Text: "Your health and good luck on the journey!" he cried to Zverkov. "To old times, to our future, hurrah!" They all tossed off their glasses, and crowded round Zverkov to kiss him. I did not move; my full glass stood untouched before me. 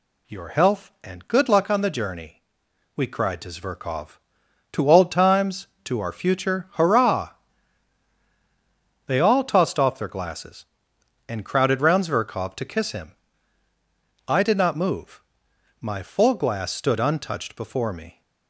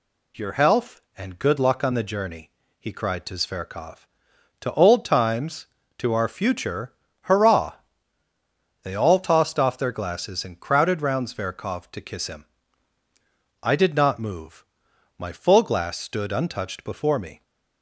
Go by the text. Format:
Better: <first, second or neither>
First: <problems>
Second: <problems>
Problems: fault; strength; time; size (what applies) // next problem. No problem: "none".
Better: second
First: says "we" for "he"; at 2.9 s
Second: none